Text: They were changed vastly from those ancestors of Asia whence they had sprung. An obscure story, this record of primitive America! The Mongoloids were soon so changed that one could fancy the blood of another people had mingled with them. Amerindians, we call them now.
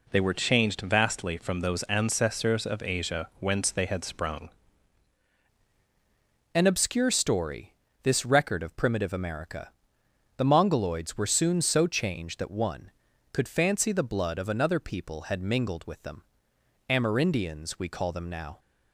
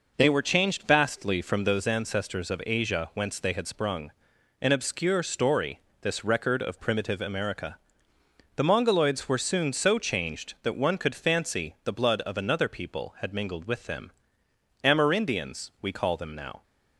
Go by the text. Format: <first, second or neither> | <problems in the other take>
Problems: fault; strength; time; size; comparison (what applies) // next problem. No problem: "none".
second | changes voice at "An"; from 6.5 s on; 12.0 s long